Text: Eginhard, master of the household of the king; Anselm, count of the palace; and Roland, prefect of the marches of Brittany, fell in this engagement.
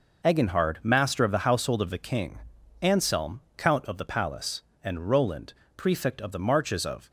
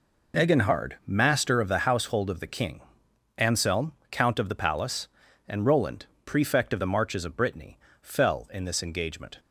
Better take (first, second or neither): second